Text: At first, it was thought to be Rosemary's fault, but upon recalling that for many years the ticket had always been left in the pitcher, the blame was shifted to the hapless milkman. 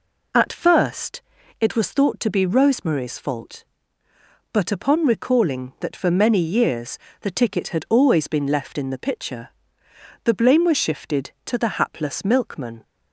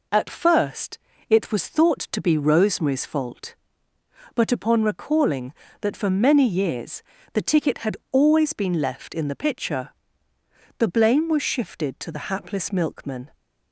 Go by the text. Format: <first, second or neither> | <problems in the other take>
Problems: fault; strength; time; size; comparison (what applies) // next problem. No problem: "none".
neither | pauses between "years" and "the"; slight; the same in both